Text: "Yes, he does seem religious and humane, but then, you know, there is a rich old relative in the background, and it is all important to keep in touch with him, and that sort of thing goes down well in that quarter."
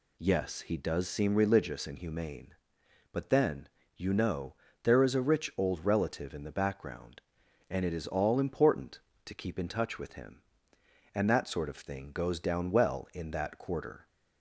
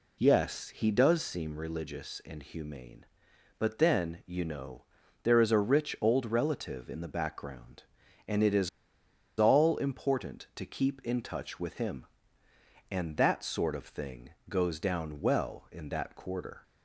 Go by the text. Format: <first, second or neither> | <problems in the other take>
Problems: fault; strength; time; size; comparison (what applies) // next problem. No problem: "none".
first | pauses between "is" and "all"; noticeable; at 8.6 s; 0.71 s long // pauses between "thing" and "goes"; slight; at 14.3 s; 0.18 s long